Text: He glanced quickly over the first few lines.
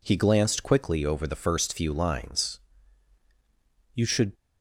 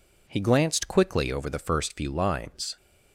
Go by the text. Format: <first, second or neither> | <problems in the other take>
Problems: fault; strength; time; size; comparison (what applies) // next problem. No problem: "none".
second | goes on to say "You should"; slight; from 3.9 s on; 0.38 s long